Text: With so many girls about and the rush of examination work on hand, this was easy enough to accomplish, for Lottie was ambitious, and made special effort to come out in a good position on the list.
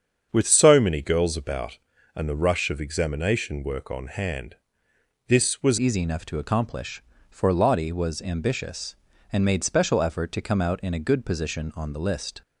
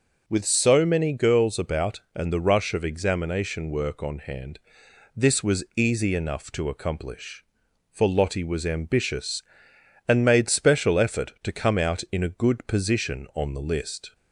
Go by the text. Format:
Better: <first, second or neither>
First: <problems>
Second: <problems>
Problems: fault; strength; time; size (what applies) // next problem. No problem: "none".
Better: second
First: starts louder than the rest; strong; until 1.3 s; 7.5 dB // changes voice at "easy"; from 5.7 s on; 6.7 s long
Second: none